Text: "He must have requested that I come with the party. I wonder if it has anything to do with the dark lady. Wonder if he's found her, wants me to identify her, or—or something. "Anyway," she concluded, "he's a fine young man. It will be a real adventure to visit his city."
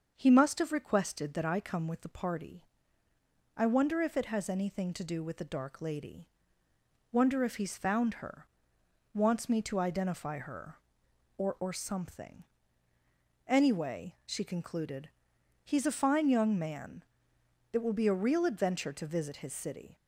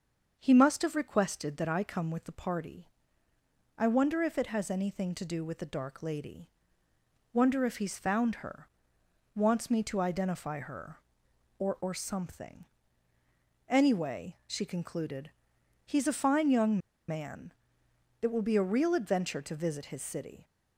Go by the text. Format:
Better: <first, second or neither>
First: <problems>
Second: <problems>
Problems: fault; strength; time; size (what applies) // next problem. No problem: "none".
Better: first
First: starts louder than the rest; until 1.1 s; 6.5 dB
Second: starts louder than the rest; until 1.3 s; 6.5 dB // pauses between "young" and "man"; slight; at 16.7 s; 0.30 s long